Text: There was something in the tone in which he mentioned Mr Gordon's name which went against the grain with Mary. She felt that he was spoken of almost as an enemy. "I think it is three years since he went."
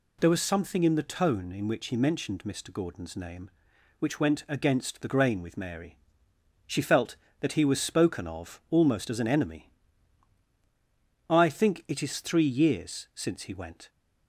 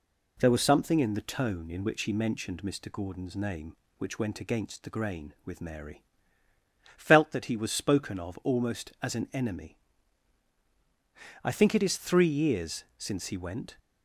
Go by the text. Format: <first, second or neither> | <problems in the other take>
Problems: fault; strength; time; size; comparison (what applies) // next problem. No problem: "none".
first | skips "She"; at 6.4 s